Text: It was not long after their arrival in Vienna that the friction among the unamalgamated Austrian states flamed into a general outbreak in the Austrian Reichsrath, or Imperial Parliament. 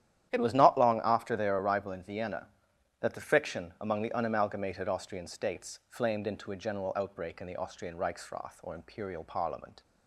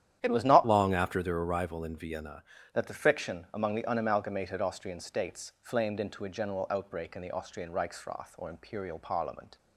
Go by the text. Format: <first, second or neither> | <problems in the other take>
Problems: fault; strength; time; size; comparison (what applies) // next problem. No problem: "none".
first | starts louder than the rest; strong; until 1.2 s; 10.5 dB; strong in the first // changes voice from "long" to "Vienna"; from 0.6 to 2.4 s; 1.8 s long